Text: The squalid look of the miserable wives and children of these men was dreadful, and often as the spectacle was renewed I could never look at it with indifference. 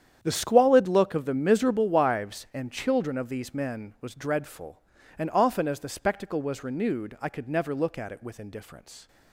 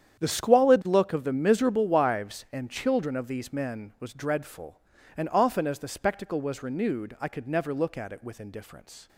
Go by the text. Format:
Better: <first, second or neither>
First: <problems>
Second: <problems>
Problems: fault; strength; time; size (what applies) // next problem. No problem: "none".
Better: neither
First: starts louder than the rest; strong; until 1.2 s; 9 dB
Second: starts louder than the rest; strong; until 1.2 s; 9 dB